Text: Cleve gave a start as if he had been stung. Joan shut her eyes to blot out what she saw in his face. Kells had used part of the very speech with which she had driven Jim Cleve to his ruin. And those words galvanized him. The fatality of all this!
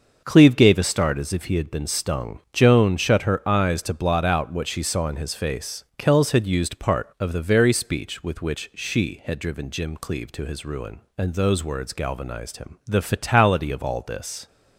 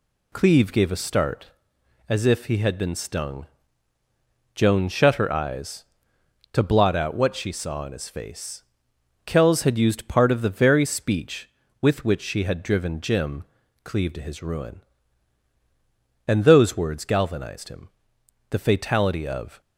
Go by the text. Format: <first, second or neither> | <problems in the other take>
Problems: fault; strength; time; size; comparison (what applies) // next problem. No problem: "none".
first | pauses between "Jim" and "Cleve"; at 13.4 s; 0.40 s long // stops before "all this"; at 19.6 s